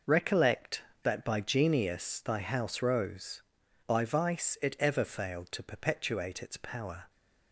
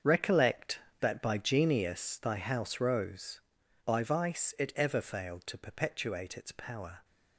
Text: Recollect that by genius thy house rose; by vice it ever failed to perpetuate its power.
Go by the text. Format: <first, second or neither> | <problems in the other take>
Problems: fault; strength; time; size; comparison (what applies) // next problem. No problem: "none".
first | gets quieter; strong; throughout; 13 dB